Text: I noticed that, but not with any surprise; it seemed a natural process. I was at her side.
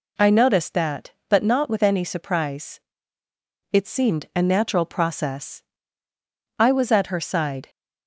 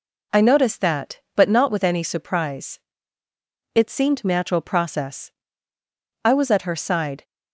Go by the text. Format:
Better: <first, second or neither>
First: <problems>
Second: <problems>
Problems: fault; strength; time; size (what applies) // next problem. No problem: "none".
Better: first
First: none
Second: skips "a"; at 4.2 s